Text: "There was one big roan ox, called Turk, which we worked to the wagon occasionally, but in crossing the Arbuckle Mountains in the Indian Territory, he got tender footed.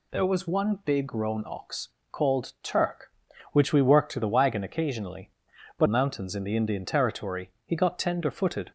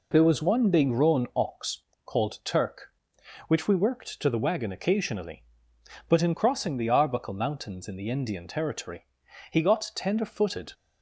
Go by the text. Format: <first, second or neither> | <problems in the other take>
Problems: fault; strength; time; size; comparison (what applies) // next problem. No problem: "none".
second | skips "in crossing the Arbuckle"; at 5.8 s